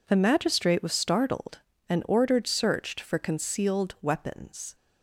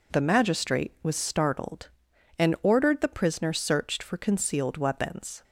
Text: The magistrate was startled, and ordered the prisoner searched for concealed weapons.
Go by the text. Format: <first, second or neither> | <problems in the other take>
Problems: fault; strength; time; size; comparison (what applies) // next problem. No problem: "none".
second | skips "the prisoner"; at 2.4 s